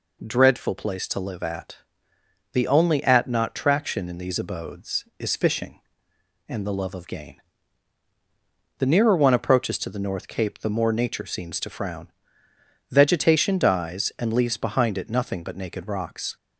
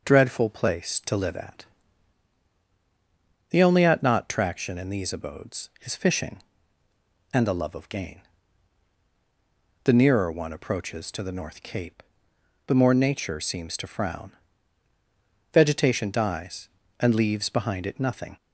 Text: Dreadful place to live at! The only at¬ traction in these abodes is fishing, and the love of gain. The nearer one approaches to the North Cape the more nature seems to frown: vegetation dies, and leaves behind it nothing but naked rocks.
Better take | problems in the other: first | pauses between "Cape" and "the"; noticeable; at 12.0 s; 0.64 s long // stops before "but naked rocks"; at 18.3 s

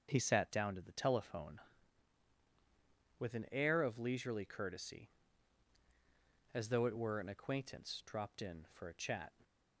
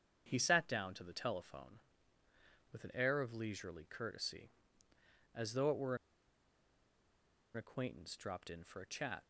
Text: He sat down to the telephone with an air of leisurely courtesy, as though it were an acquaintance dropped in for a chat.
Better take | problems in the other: first | starts louder than the rest; strong; until 1.2 s; 7.5 dB; also in the first // pauses between "were" and "an"; strong; at 5.9 s; 1.5 s long

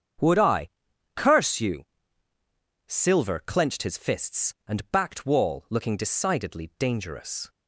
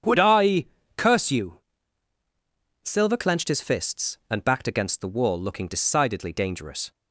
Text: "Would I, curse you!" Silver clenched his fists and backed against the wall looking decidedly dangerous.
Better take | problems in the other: second | starts louder than the rest; strong; until 1.7 s; 7.5 dB; strong in the second // skips "against the"; at 5.2 s

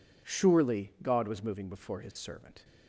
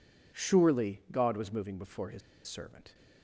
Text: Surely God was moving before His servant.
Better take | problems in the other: first | pauses between "His" and "servant"; slight; at 2.2 s; 0.27 s long

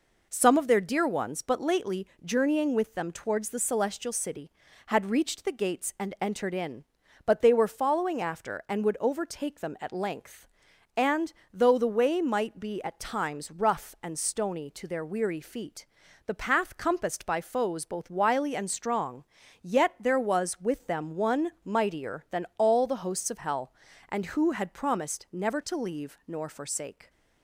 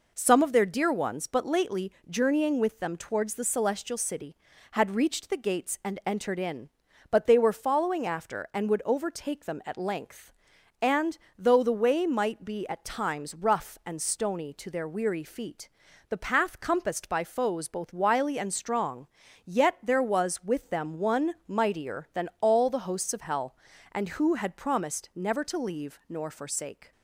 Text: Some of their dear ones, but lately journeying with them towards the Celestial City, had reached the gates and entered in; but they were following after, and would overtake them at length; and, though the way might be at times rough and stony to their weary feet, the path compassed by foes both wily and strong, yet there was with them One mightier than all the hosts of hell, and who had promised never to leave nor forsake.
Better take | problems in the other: neither | pauses between "lately" and "journeying"; slight; the same in both

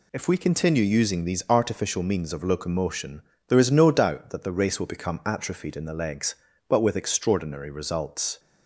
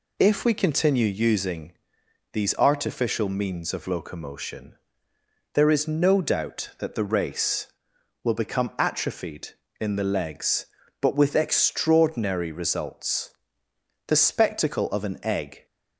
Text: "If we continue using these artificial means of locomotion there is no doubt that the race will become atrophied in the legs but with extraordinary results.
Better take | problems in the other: first | pauses between "using" and "these"; noticeable; at 1.7 s; 0.58 s long // pauses between "locomotion" and "there"; noticeable; at 4.7 s; 0.78 s long; slight in the first // goes on to say "The spectacle of an egg"; from 14.0 s on; 1.5 s long

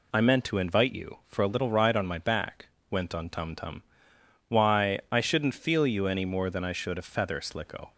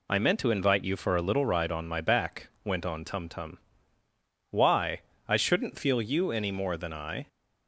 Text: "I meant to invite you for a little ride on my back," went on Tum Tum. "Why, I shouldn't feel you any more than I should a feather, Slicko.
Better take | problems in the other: first | stops before "should a feather Slicko"; at 7.2 s

